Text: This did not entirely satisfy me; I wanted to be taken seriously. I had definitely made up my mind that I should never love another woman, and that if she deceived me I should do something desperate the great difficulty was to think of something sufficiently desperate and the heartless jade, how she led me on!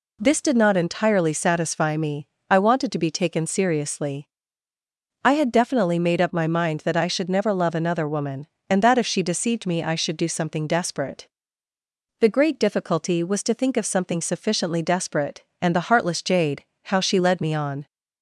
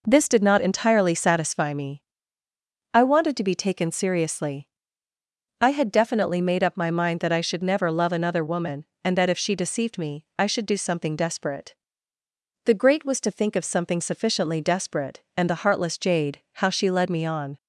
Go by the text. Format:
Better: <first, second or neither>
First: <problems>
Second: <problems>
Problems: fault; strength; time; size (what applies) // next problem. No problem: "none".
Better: first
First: pauses between "desperate" and "the"; noticeable; at 11.2 s; 0.92 s long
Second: pauses between "desperate" and "the"; noticeable; at 11.7 s; 0.90 s long // skips "difficulty"; at 13.0 s